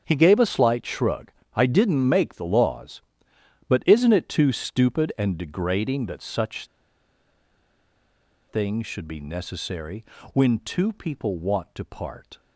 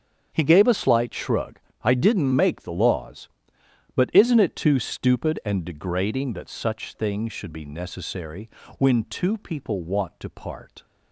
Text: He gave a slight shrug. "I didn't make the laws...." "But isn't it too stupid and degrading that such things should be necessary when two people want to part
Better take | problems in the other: second | starts louder than the rest; strong; until 1.0 s; 7.5 dB; strong in the second // pauses between "such" and "things"; strong; at 6.6 s; 1.8 s long // pauses between "necessary" and "when"; slight; at 10.0 s; 0.30 s long; slight in the second

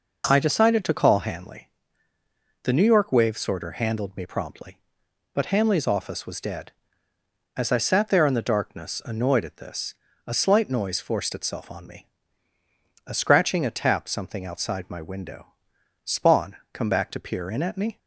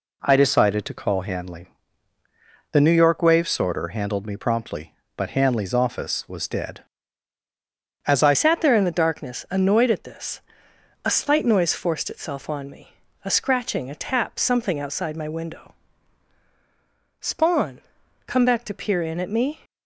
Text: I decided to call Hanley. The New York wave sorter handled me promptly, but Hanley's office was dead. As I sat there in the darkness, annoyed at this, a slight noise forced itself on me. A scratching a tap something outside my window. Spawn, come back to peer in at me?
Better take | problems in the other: first | changes voice at "sat"; from 8.3 s on; 11.2 s long

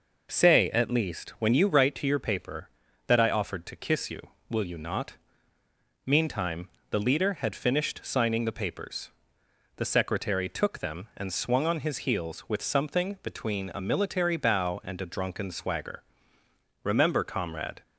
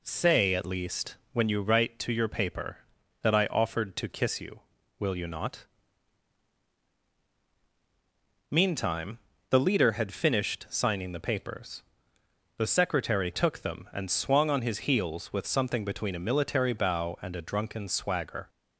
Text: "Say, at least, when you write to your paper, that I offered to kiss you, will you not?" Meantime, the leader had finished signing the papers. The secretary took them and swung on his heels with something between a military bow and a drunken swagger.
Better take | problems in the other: second | goes on to say "Remember comrade"; noticeable; from 16.8 s on; 0.98 s long

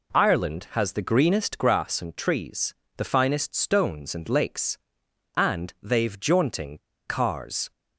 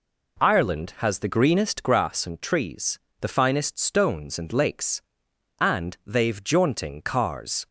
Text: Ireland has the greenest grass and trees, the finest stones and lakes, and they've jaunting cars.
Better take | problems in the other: second | pauses between "jaunting" and "cars"; slight; at 6.7 s; 0.30 s long

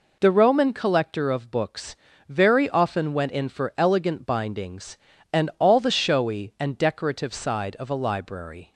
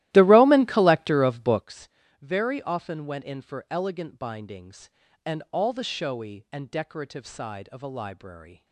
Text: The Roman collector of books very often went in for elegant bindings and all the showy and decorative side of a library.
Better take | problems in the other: first | starts louder than the rest; strong; until 1.7 s; 15.5 dB // pauses between "books" and "very"; slight; at 1.8 s; 0.32 s long; slight in the first

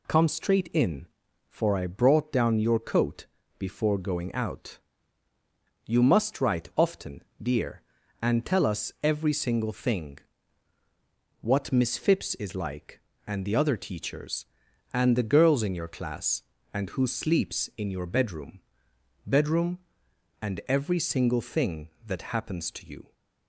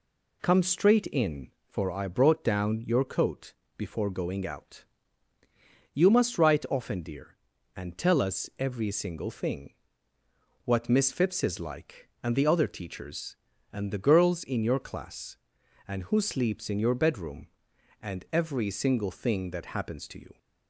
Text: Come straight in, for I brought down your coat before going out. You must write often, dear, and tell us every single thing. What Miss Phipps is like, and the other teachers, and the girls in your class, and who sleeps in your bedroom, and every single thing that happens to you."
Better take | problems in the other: second | pauses between "coat" and "before"; slight; at 3.2 s; 0.32 s long; slight in the second // says "bedroom" twice; at 19.2 s

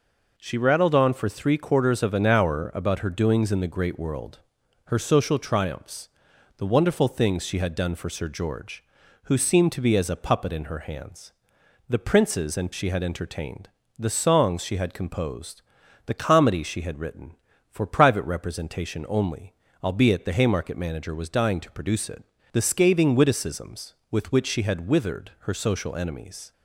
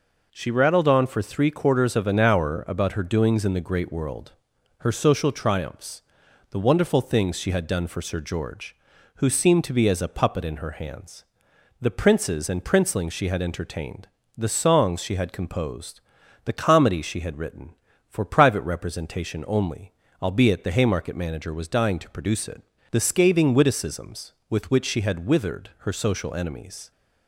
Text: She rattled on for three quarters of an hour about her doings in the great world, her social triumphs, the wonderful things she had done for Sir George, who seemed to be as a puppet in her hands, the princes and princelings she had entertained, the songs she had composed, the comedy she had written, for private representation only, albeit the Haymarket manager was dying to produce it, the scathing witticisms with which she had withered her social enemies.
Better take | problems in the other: second | skips "princelings"; at 12.7 s

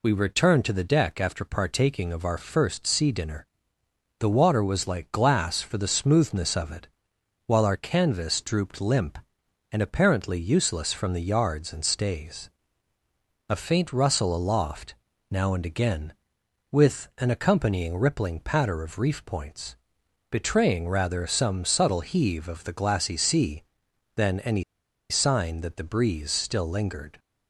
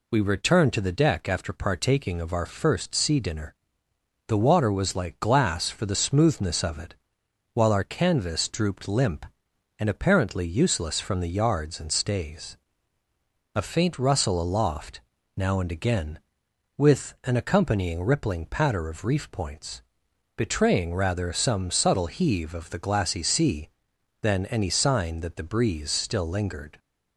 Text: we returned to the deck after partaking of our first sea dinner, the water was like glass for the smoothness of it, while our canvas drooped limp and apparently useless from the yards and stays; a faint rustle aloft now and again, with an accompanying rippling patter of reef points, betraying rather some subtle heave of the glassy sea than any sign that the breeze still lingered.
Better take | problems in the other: second | pauses between "aloft" and "now"; at 14.9 s; 0.38 s long; also in the second // pauses between "any" and "sign"; noticeable; at 24.6 s; 0.47 s long

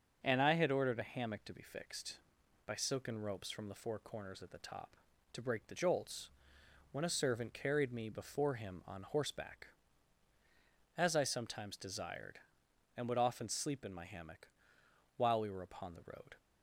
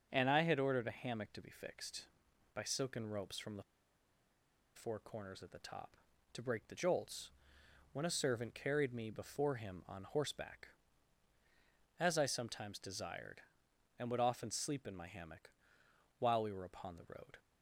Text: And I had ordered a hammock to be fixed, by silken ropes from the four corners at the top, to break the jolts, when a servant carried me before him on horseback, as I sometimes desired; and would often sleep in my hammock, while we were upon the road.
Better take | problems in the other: first | starts louder than the rest; until 1.1 s; 6.5 dB; also in the first // pauses between "the" and "four"; at 3.6 s; 1.1 s long

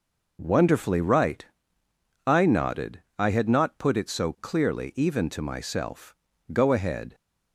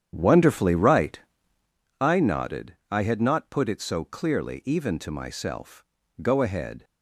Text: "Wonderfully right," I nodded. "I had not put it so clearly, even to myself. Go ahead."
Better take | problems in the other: first | starts louder than the rest; strong; until 1.8 s; 9 dB

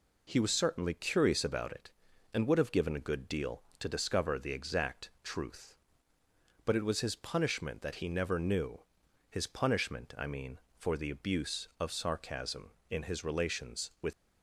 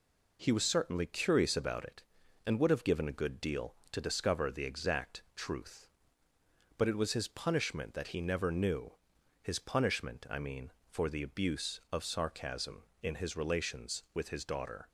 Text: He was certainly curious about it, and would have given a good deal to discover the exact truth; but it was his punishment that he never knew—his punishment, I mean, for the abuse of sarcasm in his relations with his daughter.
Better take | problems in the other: second | stops before "his daughter"; at 14.1 s

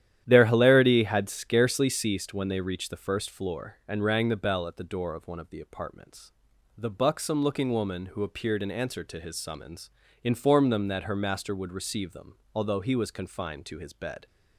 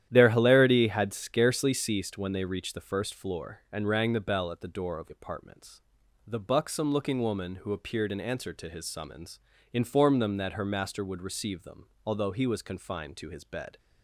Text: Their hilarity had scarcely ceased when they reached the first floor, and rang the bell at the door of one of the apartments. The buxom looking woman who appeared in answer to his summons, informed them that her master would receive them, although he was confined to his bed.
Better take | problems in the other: first | starts louder than the rest; strong; until 1.1 s; 11 dB; strong in the first // skips "one of the"; at 5.0 s

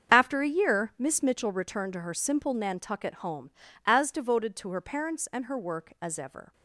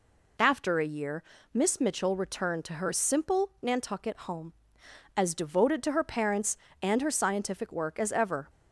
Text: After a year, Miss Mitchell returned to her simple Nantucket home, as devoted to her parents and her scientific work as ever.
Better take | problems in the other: second | starts louder than the rest; until 1.1 s; 6.5 dB // skips "scientific"; at 5.5 s

